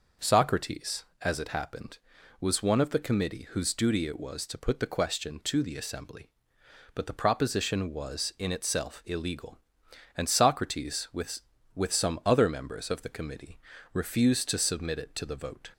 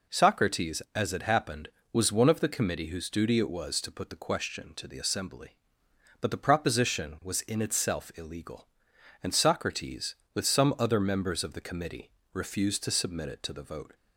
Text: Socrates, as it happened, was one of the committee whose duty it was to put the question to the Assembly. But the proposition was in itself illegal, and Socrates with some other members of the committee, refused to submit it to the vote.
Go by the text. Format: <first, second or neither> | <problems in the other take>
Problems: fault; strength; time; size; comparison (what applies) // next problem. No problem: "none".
second | says "with" twice; at 11.7 s